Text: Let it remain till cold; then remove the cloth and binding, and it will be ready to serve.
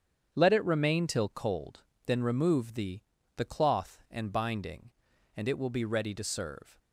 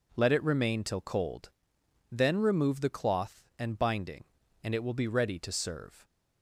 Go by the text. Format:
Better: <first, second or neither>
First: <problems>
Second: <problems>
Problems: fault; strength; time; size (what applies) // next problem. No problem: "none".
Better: second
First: starts louder than the rest; strong; until 1.3 s; 8 dB // says "the" twice; at 3.3 s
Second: none